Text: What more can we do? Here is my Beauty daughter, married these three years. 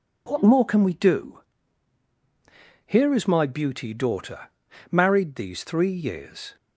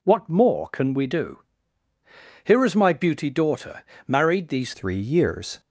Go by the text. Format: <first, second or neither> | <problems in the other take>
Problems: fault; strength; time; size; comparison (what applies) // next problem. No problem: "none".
first | changes voice at "three"; from 4.7 s on; 0.8 s long